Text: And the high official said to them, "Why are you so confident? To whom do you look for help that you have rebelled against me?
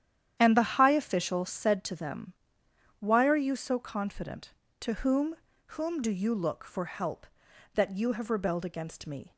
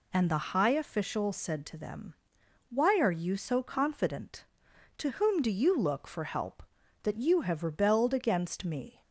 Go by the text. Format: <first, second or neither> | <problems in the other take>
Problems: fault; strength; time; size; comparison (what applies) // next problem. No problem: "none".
second | starts louder than the rest; strong; until 1.4 s; 10 dB // says "whom" twice; at 5.7 s